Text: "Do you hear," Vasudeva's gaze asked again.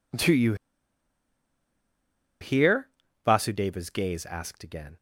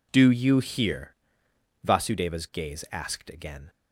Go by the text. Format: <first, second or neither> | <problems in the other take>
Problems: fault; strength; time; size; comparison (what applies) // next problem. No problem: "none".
second | pauses between "you" and "hear"; strong; at 0.5 s; 1.8 s long